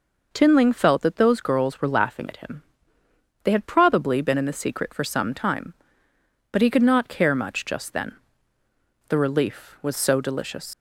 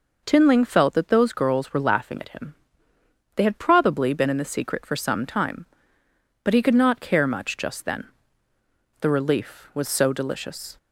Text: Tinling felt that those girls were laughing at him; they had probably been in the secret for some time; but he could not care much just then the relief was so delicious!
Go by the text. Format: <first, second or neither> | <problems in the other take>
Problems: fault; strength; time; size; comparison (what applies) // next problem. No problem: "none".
second | pauses between "then" and "the"; noticeable; at 8.1 s; 0.94 s long; noticeable in the second // leaves "delicious" unfinished; at 10.7 s; 115 ms